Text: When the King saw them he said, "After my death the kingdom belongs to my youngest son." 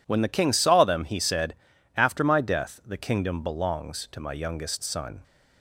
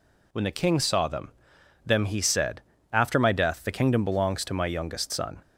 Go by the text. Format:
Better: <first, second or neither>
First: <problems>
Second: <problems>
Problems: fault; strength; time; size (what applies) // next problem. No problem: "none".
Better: first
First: none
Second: says "them" twice; at 1.8 s